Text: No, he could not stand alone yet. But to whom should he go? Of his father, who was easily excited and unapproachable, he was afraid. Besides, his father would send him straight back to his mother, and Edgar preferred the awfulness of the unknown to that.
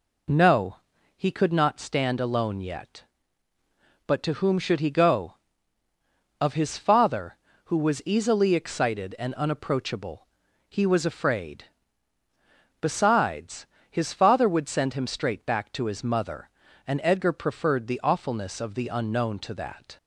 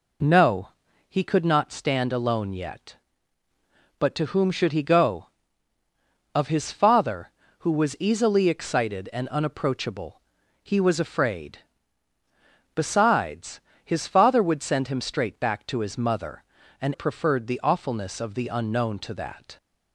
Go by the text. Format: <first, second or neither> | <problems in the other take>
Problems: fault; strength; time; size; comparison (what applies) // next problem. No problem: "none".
first | skips "Edgar"; at 16.9 s